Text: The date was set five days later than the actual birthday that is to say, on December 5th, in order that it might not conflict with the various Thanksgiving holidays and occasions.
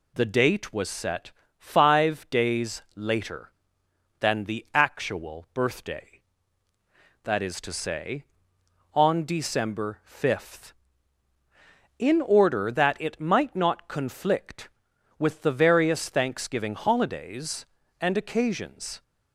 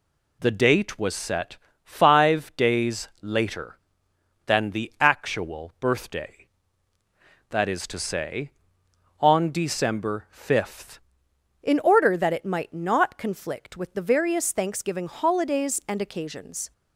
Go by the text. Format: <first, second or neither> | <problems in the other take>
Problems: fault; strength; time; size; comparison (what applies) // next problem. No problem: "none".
first | pauses between "set" and "five"; slight; at 1.5 s; 0.26 s long; slight in the first // changes voice at "in"; from 11.6 s on; 5.1 s long